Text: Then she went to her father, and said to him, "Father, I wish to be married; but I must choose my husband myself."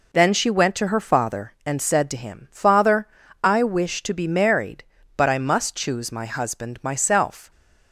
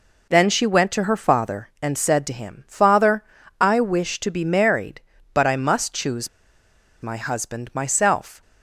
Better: first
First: none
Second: pauses between "choose" and "my"; noticeable; at 6.2 s; 0.74 s long

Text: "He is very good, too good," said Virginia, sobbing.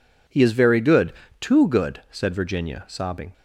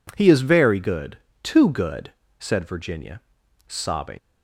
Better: first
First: none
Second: leaves "sobbing" unfinished; at 4.1 s; 110 ms

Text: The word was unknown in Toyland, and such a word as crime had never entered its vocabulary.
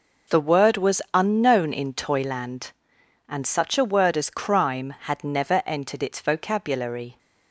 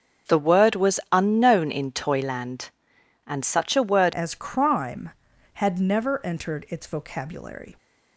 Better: first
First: none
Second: starts louder than the rest; until 1.4 s; 7 dB // changes voice at "as"; from 4.1 s on; 3.6 s long

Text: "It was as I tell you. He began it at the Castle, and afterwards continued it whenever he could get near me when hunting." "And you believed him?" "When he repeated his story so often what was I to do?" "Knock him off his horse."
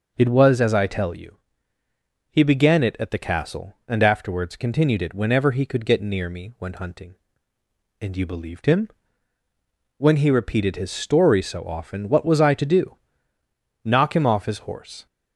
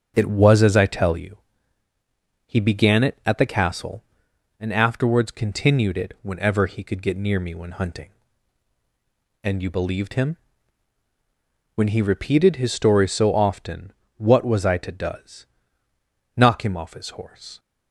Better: first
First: none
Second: starts louder than the rest; strong; until 1.1 s; 7.5 dB // pauses between "often" and "what"; slight; at 13.9 s; 0.24 s long // says "does" for "do"; at 14.9 s

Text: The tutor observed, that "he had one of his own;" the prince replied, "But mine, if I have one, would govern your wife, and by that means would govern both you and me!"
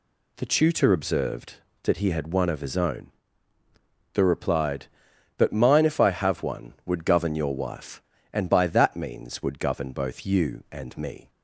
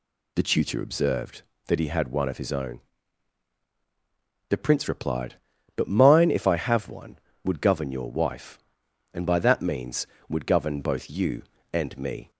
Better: second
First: skips "prince"; at 4.2 s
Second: none

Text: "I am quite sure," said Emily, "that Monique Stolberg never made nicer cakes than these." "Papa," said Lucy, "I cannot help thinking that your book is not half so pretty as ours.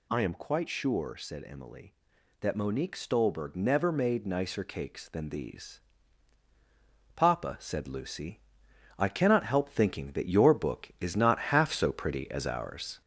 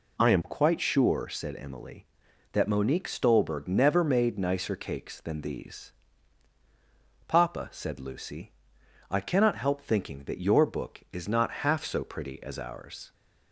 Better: second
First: gets louder; noticeable; throughout; 4.5 dB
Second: none

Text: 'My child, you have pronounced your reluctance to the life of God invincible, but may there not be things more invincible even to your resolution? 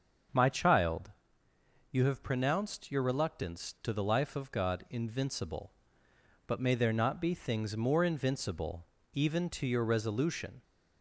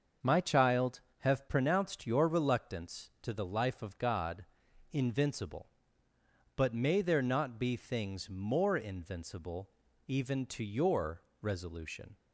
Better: first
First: starts louder than the rest; until 2.1 s; 7 dB // pauses between "invincible" and "even"; slight; at 8.8 s; 0.28 s long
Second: starts louder than the rest; until 1.4 s; 6.5 dB // skips "you"; at 1.0 s // pauses between "God" and "invincible"; noticeable; at 4.4 s; 0.46 s long // pauses between "invincible" and "even"; at 9.6 s; 0.38 s long // pauses between "your" and "resolution"; slight; at 11.2 s; 0.20 s long

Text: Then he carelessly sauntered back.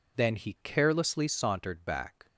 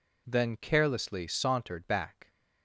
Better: first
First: none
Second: skips "he"; at 0.5 s

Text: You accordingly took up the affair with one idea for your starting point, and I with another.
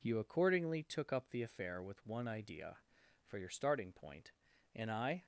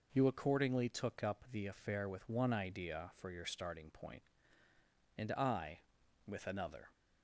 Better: second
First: stops before "with another"; at 5.2 s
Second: none

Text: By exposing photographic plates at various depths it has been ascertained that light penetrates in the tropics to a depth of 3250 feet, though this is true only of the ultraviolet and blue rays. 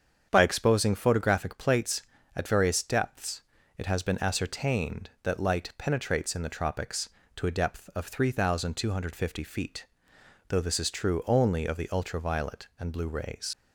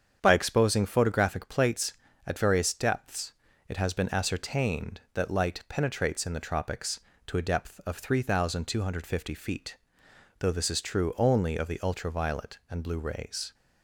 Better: second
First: starts louder than the rest; strong; until 1.3 s; 7.5 dB // pauses between "depths" and "it"; at 3.4 s; 0.38 s long // leaves "rays" unfinished; at 13.5 s; 95 ms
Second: starts louder than the rest; strong; until 1.2 s; 8 dB // pauses between "depths" and "it"; at 3.3 s; 0.38 s long

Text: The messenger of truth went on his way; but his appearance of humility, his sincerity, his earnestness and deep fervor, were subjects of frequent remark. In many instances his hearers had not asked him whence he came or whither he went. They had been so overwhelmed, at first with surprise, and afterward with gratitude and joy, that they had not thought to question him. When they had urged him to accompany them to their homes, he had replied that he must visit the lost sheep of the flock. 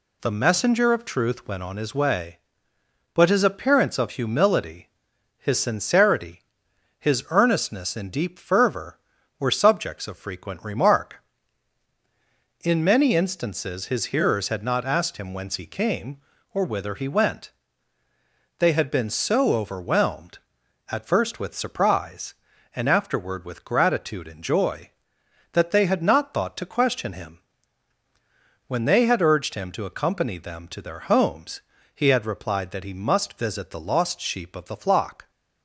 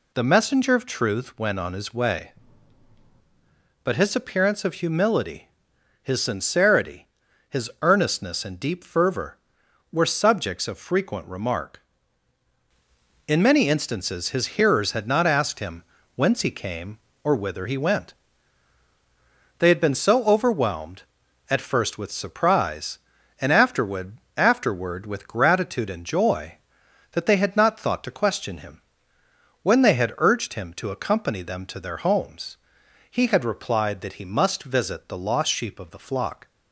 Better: first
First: none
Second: pauses between "him" and "whence"; slight; at 15.8 s; 0.32 s long // says "afterward" twice; at 24.3 s

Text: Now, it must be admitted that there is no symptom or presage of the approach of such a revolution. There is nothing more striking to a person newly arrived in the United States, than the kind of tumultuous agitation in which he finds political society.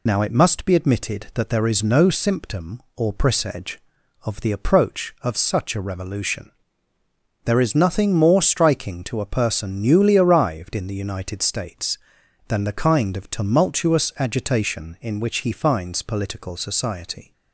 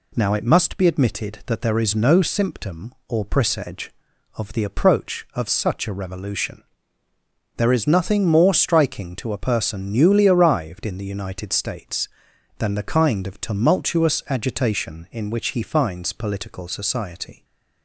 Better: second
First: loses the start of "Now"; at 0.0 s; 50 ms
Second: none

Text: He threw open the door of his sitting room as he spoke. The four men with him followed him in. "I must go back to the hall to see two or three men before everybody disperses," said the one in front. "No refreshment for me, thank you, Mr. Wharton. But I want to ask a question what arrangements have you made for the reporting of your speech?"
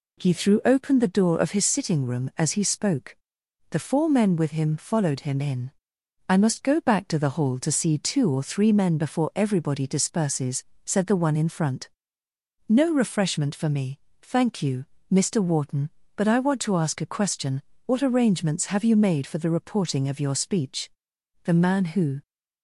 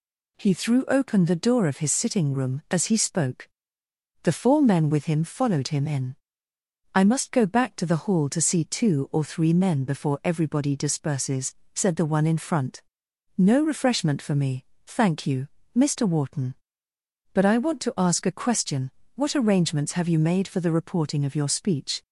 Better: second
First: pauses between "question" and "what"; slight; at 17.6 s; 0.24 s long // goes on to say "The man who"; noticeable; from 21.4 s on; 0.78 s long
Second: pauses between "question" and "what"; slight; at 18.8 s; 0.26 s long

